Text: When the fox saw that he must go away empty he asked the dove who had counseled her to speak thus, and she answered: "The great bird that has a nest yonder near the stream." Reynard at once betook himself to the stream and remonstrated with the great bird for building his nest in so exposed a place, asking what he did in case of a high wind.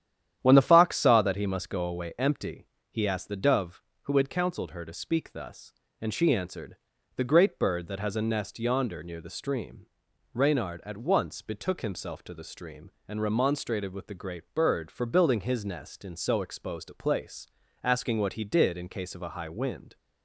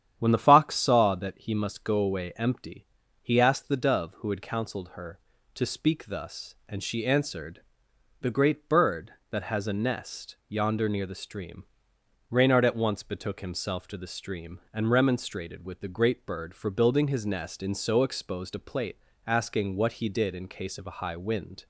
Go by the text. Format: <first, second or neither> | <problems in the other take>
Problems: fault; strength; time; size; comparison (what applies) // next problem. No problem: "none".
first | starts louder than the rest; strong; until 1.1 s; 9.5 dB; strong in the first // pauses between "empty" and "he"; slight; at 2.8 s; 0.36 s long; slight in the first // says "plate" for "place"; at 18.5 s